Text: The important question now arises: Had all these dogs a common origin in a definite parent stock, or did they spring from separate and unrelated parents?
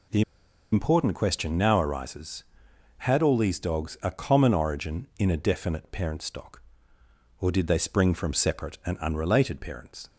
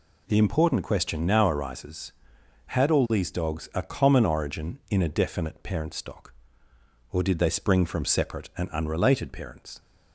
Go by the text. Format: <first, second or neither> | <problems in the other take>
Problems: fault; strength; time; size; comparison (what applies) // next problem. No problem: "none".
second | pauses between "The" and "important"; noticeable; at 0.2 s; 0.50 s long